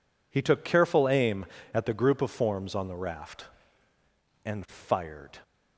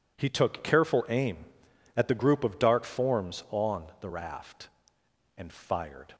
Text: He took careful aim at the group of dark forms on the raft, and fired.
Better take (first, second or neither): second